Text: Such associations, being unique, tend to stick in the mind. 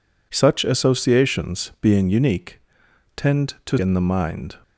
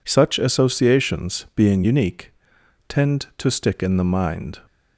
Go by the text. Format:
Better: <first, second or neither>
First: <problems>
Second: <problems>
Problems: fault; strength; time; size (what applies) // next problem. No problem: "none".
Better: second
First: skips "stick"; at 3.7 s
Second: none